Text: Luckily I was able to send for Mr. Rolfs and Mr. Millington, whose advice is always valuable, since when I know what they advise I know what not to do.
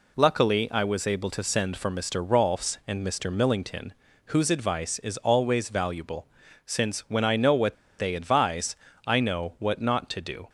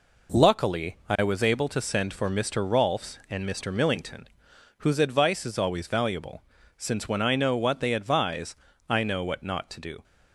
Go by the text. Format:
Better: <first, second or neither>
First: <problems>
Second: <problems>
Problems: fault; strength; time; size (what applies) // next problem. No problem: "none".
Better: second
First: pauses between "what" and "they"; slight; at 7.7 s; 0.24 s long // pauses between "advise" and "I"; slight; at 8.7 s; 0.32 s long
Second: pauses between "advise" and "I"; slight; at 8.5 s; 0.34 s long